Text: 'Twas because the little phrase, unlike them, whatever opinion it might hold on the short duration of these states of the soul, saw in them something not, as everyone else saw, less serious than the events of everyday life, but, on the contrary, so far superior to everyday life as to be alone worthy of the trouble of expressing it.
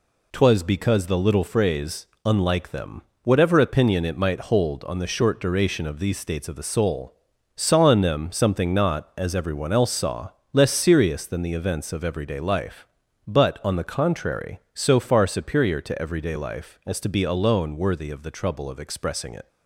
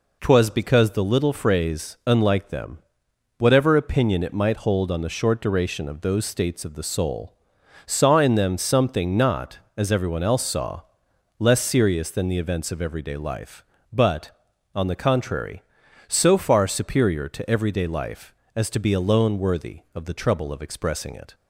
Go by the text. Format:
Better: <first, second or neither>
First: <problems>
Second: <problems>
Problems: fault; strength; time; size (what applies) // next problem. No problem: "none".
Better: first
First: none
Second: says "those" for "these"; at 6.0 s